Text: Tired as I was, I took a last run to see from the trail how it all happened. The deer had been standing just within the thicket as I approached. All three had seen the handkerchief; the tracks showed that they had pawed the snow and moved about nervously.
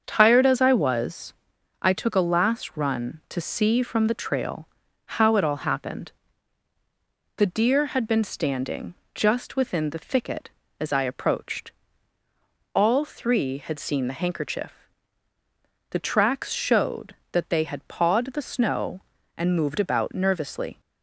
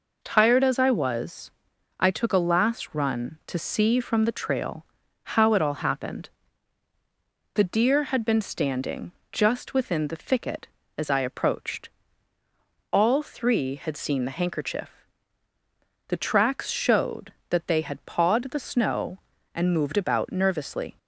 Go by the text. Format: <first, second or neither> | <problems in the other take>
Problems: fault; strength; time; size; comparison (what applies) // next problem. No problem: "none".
second | starts louder than the rest; until 1.5 s; 7 dB // pauses between "trail" and "how"; at 4.6 s; 0.38 s long; also in the second // pauses between "standing" and "just"; slight; at 8.9 s; 0.20 s long; slight in the second